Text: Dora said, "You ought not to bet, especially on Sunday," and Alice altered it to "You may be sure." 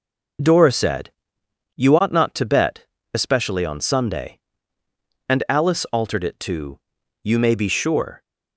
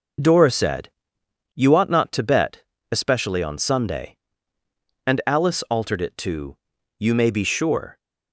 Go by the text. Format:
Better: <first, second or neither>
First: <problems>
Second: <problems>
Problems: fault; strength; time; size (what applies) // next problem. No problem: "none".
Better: neither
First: pauses between "to" and "You"; at 6.7 s; 0.42 s long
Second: pauses between "to" and "You"; at 6.5 s; 0.40 s long